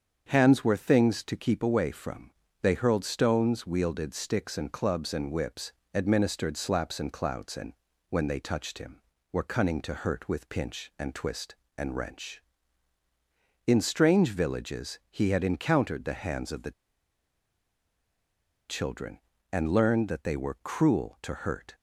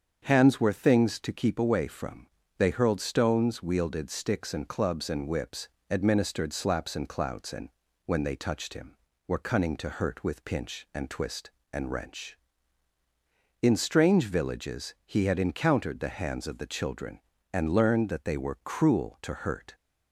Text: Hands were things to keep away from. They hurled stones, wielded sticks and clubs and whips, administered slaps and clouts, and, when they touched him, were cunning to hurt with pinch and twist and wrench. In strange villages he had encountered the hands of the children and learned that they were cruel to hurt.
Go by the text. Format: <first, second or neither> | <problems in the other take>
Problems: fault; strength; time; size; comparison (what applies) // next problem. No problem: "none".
second | starts louder than the rest; strong; until 1.2 s; 7.5 dB; strong in the second // pauses between "the" and "children"; strong; at 16.7 s; 1.9 s long